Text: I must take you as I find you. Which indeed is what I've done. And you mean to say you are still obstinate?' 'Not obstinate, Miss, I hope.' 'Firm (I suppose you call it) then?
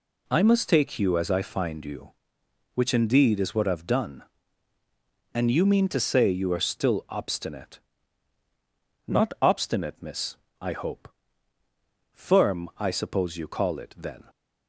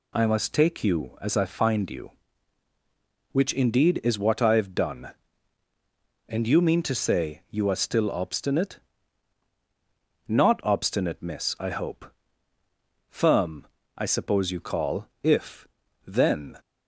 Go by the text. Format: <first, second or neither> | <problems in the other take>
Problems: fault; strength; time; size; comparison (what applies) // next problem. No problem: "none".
first | says "if" for "it"; at 15.2 s